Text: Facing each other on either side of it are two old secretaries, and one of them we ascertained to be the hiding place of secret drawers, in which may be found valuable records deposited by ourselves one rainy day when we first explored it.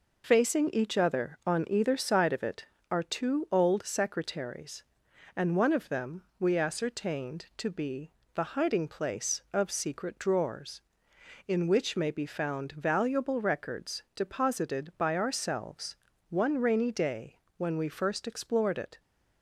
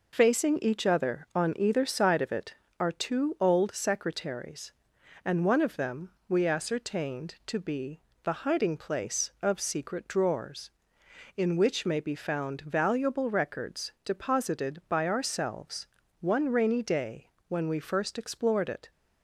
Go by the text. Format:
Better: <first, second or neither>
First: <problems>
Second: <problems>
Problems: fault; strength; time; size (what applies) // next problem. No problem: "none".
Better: neither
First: pauses between "them" and "we"; slight; at 6.2 s; 0.16 s long // pauses between "be" and "the"; slight; at 8.0 s; 0.24 s long // pauses between "ourselves" and "one"; slight; at 15.9 s; 0.34 s long // pauses between "day" and "when"; slight; at 17.3 s; 0.20 s long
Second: pauses between "them" and "we"; slight; at 6.1 s; 0.18 s long // pauses between "be" and "the"; slight; at 7.9 s; 0.24 s long // pauses between "ourselves" and "one"; slight; at 15.8 s; 0.34 s long // pauses between "day" and "when"; slight; at 17.2 s; 0.20 s long